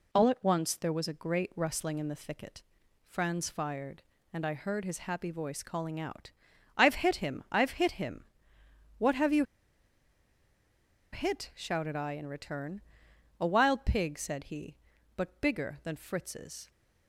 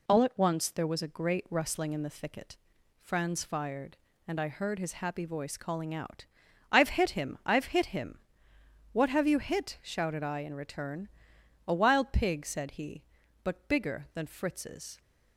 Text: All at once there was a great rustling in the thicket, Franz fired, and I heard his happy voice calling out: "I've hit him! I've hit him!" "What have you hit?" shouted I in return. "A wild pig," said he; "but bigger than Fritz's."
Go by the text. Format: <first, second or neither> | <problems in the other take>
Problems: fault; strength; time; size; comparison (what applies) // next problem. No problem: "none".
second | pauses between "you" and "hit"; strong; at 9.4 s; 1.6 s long